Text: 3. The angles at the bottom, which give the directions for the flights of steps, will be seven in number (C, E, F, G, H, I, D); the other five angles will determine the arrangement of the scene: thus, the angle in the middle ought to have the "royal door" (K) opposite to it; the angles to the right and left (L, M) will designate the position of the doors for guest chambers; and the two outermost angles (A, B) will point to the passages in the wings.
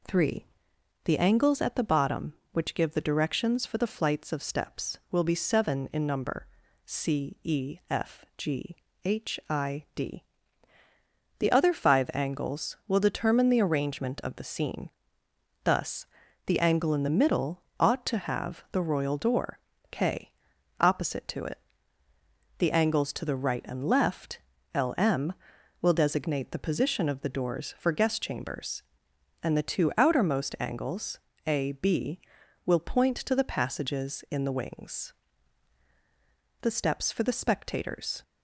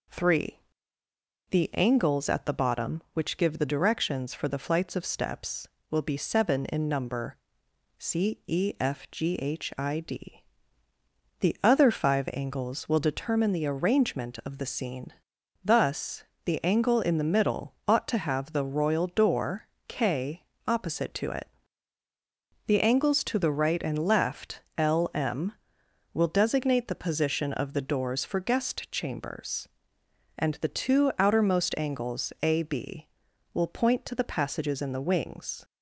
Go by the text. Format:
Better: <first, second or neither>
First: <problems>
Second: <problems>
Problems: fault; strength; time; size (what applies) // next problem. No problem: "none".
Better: second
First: pauses between "middle" and "ought"; slight; at 17.6 s; 0.16 s long // pauses between "door" and "K"; slight; at 19.5 s; 0.32 s long // goes on to say "The steps for the spectators"; from 36.6 s on; 1.6 s long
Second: pauses between "door" and "K"; slight; at 19.6 s; 0.18 s long